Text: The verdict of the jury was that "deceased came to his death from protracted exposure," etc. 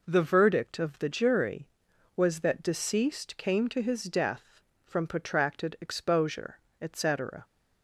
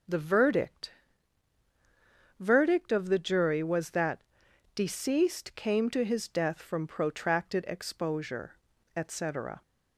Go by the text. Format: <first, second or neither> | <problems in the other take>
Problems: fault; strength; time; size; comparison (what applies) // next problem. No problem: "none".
first | says "verdict" twice; at 2.3 s // pauses between "that" and "deceased"; noticeable; at 4.2 s; 0.52 s long